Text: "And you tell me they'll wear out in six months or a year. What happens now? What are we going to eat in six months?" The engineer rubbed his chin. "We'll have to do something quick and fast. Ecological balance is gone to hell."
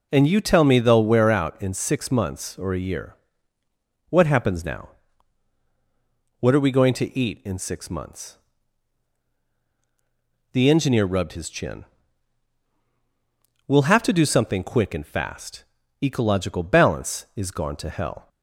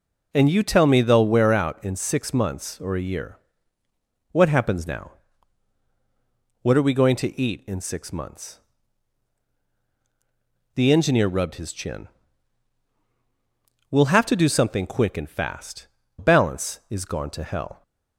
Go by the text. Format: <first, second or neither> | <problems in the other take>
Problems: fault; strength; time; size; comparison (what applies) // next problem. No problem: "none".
first | skips "Ecological"; at 16.0 s